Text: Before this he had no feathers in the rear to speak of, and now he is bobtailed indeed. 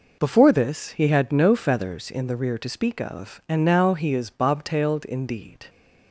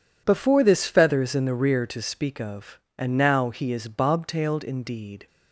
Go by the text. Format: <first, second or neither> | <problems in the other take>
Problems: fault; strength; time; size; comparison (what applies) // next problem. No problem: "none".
first | skips "he had no"; at 0.8 s